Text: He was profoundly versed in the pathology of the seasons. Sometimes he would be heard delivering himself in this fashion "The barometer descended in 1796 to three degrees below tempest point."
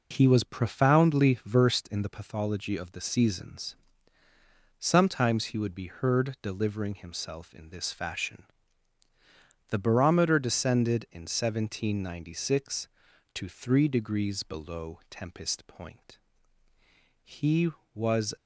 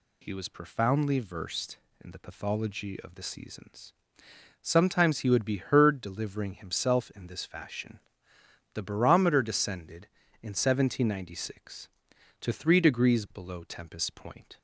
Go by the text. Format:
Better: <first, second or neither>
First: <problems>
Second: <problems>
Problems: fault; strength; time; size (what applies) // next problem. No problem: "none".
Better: second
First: pauses between "fashion" and "The"; at 8.4 s; 1.2 s long // pauses between "below" and "tempest"; slight; at 14.9 s; 0.16 s long // goes on to say "He was"; noticeable; from 17.2 s on; 1.1 s long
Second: pauses between "fashion" and "The"; noticeable; at 7.9 s; 0.76 s long